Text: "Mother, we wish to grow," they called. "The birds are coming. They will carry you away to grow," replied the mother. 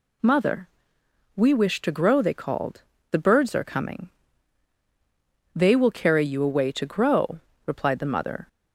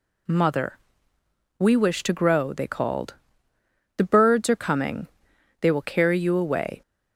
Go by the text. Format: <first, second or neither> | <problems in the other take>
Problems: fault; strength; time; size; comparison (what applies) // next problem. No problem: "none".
first | stops before "to grow replied the mother"; at 6.8 s